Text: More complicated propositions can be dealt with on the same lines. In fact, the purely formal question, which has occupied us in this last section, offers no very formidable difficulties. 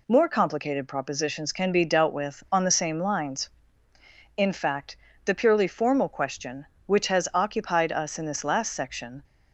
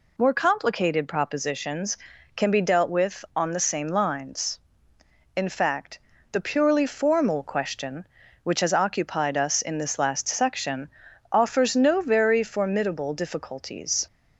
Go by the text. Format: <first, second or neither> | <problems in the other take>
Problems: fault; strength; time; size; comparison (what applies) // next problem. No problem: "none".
second | stops before "offers no very formidable difficulties"; at 9.2 s